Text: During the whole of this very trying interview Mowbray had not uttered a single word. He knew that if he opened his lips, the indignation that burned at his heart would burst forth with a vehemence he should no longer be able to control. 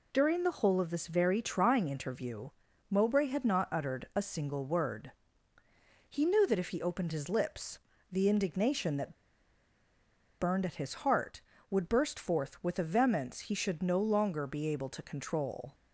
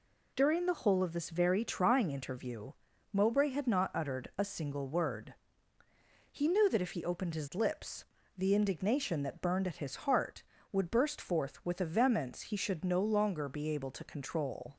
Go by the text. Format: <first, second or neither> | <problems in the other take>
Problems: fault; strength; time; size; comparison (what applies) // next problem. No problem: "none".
second | pauses between "interview" and "Mowbray"; at 2.4 s; 0.42 s long; also in the second // pauses between "that" and "burned"; strong; at 9.1 s; 1.2 s long